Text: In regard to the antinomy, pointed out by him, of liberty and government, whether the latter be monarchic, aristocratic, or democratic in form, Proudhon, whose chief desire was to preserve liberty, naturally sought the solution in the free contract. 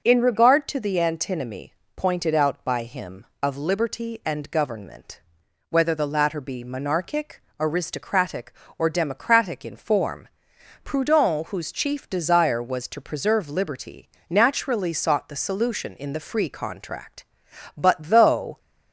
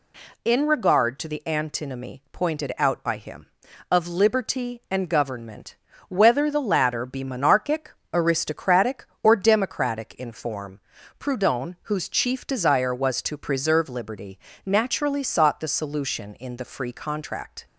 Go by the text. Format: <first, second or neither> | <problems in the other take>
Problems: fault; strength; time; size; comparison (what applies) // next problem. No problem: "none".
second | goes on to say "But though"; noticeable; from 17.7 s on; 0.82 s long